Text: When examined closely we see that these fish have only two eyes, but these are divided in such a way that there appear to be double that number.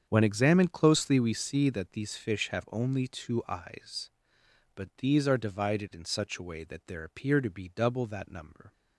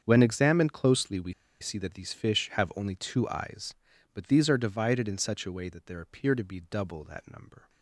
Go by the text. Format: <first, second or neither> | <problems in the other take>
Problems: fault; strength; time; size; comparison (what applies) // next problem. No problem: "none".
first | starts louder than the rest; strong; until 1.0 s; 7.5 dB; strong in the first // pauses between "we" and "see"; slight; at 1.3 s; 0.28 s long